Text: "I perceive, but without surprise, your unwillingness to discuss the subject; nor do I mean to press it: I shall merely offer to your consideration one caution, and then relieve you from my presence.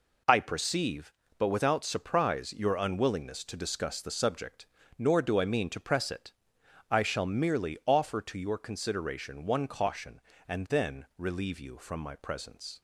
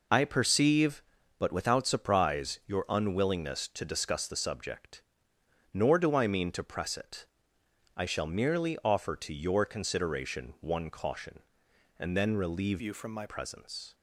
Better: first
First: none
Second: changes voice from "you" to "my"; from 12.7 to 13.2 s; 0.5 s long

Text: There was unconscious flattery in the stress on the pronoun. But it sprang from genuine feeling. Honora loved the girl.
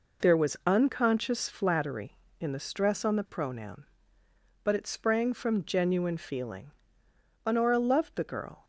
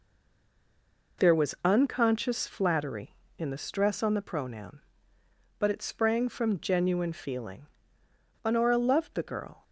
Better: first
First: none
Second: stays silent before the first word; until 1.1 s; 1.1 s long

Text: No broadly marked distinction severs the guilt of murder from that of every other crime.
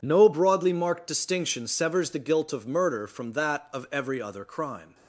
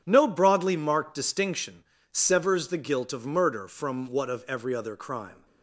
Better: first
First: none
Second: starts louder than the rest; strong; until 1.0 s; 8.5 dB // pauses between "distinction" and "severs"; slight; at 1.8 s; 0.26 s long // says "what" for "that"; at 4.0 s

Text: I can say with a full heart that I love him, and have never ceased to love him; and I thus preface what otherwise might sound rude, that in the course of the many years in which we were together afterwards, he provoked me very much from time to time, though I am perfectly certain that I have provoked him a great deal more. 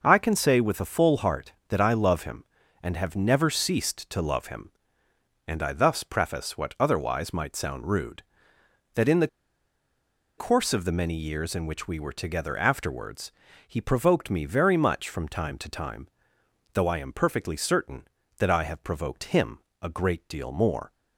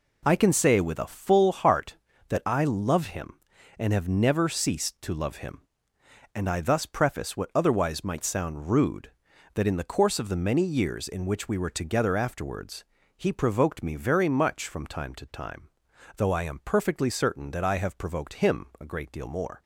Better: second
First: pauses between "the" and "course"; at 9.2 s; 1.1 s long // pauses between "him" and "a"; slight; at 19.5 s; 0.24 s long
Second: none

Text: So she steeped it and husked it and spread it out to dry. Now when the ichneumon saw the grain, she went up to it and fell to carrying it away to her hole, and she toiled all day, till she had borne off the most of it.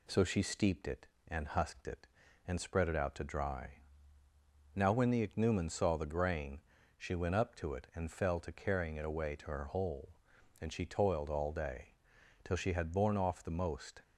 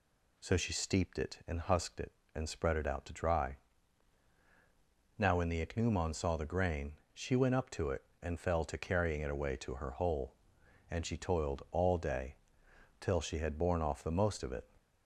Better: second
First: stops before "of it"; at 14.0 s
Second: none

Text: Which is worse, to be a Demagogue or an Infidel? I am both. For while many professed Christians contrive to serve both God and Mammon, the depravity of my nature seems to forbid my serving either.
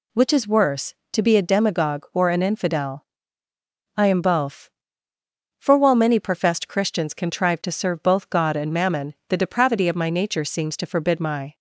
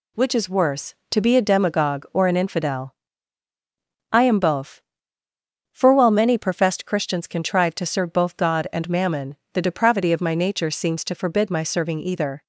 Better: second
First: stops before "serving either"; at 11.5 s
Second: none

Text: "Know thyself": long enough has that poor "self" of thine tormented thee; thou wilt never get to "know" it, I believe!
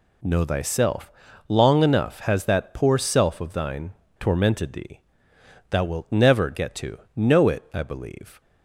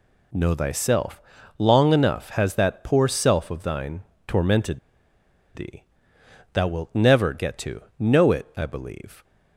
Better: first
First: pauses between "thine" and "tormented"; slight; at 3.9 s; 0.25 s long // pauses between "to" and "know"; slight; at 6.9 s; 0.16 s long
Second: pauses between "thine" and "tormented"; slight; at 4.0 s; 0.22 s long // pauses between "tormented" and "thee"; noticeable; at 4.7 s; 0.76 s long // pauses between "to" and "know"; slight; at 7.8 s; 0.16 s long

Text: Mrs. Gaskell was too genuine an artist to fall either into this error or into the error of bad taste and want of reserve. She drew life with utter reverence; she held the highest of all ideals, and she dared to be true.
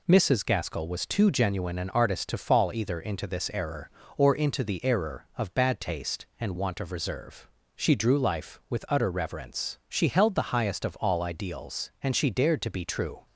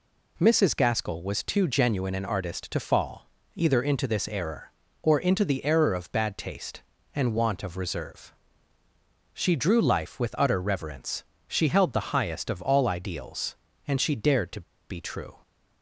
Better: first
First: none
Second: pauses between "fall" and "either"; slight; at 3.2 s; 0.28 s long // pauses between "to" and "be"; slight; at 14.6 s; 0.29 s long

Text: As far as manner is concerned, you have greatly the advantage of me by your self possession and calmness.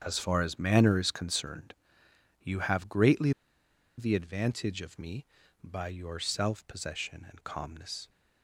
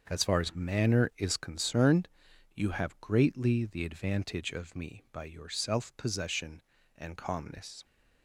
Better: second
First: starts louder than the rest; strong; until 1.0 s; 7.5 dB // pauses between "greatly" and "the"; noticeable; at 3.3 s; 0.67 s long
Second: starts louder than the rest; until 1.1 s; 6.5 dB

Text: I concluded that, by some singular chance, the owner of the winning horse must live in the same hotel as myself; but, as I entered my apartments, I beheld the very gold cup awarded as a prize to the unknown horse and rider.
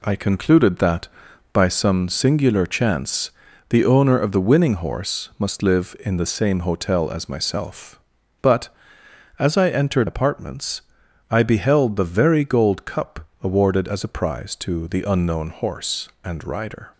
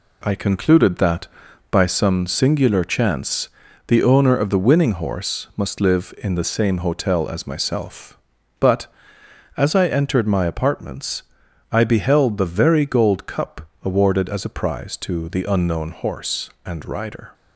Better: second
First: skips "my"; at 10.0 s // pauses between "cup" and "awarded"; slight; at 13.2 s; 0.16 s long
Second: pauses between "cup" and "awarded"; slight; at 13.6 s; 0.16 s long

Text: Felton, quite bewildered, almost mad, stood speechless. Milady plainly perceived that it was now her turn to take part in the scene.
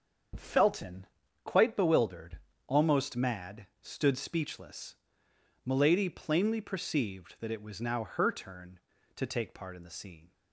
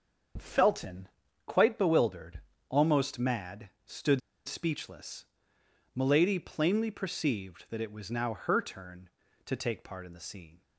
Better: first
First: starts louder than the rest; until 1.7 s; 7 dB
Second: starts louder than the rest; until 1.7 s; 7 dB // pauses between "stood" and "speechless"; slight; at 4.2 s; 0.25 s long

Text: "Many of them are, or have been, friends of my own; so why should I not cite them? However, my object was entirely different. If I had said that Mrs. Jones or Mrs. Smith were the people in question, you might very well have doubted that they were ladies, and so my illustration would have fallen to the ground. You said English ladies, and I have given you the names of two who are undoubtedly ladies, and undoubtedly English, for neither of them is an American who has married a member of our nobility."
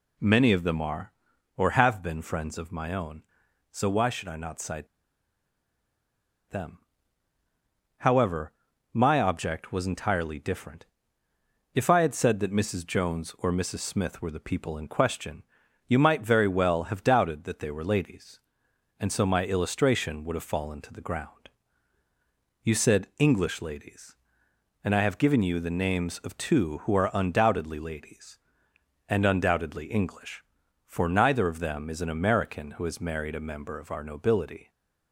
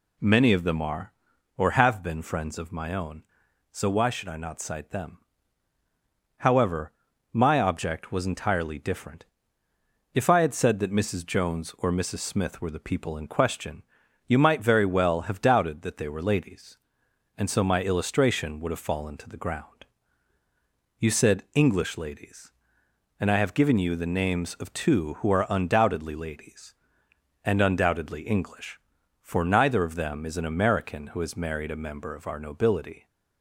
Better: second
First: pauses between "cite" and "them"; strong; at 4.8 s; 1.6 s long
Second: none

